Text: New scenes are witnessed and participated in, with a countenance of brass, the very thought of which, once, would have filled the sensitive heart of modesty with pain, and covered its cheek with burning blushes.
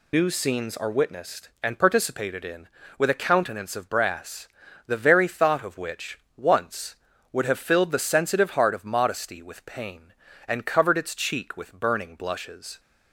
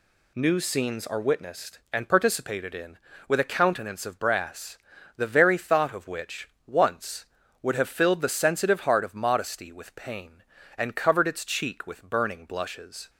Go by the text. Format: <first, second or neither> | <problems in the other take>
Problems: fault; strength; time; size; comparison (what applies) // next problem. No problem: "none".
second | loses the start of "New"; at 0.1 s; 80 ms